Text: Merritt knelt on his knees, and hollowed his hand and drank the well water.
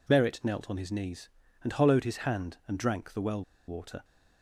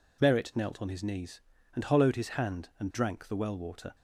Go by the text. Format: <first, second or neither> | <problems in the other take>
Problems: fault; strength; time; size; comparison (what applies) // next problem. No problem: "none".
second | pauses between "well" and "water"; slight; at 3.4 s; 0.25 s long